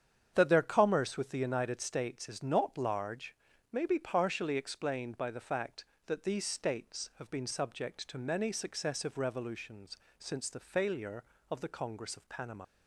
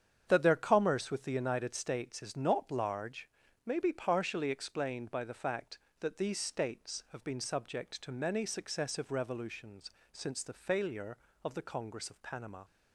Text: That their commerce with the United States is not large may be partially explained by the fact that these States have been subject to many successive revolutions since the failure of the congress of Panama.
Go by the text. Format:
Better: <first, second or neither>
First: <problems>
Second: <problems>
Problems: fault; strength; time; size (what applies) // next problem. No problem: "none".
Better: second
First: starts louder than the rest; strong; until 1.3 s; 8 dB // pauses between "large" and "may"; slight; at 3.3 s; 0.36 s long // pauses between "revolutions" and "since"; slight; at 9.9 s; 0.22 s long // leaves "Panama" unfinished; at 12.6 s; 65 ms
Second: starts louder than the rest; strong; until 1.2 s; 8 dB // pauses between "large" and "may"; slight; at 3.2 s; 0.36 s long // pauses between "revolutions" and "since"; slight; at 9.8 s; 0.22 s long